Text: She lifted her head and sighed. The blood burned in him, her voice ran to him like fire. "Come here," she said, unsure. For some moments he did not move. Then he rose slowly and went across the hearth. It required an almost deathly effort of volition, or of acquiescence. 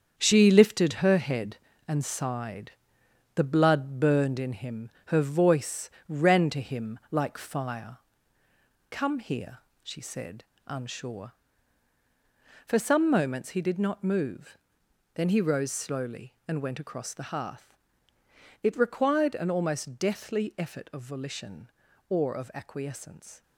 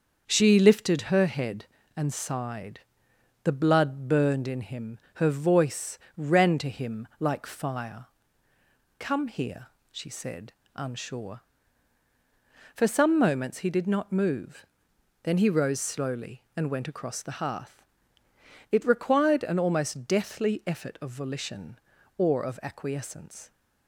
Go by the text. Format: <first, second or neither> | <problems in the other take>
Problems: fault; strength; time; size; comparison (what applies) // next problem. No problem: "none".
second | gets quieter; strong; throughout; 9 dB // starts louder than the rest; strong; until 1.1 s; 7.5 dB; also in the second // pauses between "voice" and "ran"; slight; at 5.9 s; 0.18 s long; slight in the second